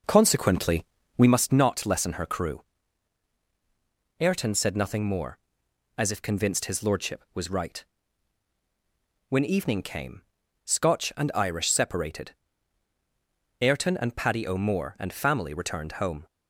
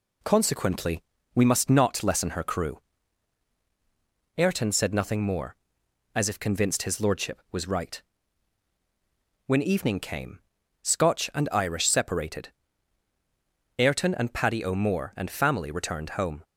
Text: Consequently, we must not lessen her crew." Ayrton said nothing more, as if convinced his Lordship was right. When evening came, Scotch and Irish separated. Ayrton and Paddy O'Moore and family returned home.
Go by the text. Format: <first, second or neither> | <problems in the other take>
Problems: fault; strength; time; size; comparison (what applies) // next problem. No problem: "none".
second | starts louder than the rest; noticeable; until 1.4 s; 5 dB